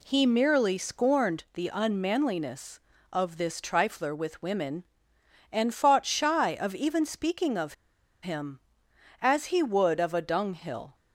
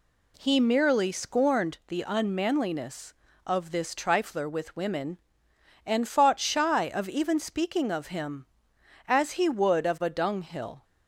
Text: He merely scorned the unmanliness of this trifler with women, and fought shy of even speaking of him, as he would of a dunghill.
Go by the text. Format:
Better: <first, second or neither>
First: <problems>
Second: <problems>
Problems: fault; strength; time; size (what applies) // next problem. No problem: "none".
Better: second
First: pauses between "of" and "him"; noticeable; at 7.7 s; 0.49 s long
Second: none